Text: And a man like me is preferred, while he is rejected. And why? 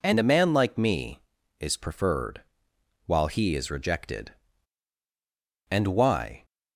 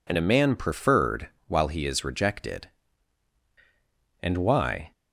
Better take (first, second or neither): first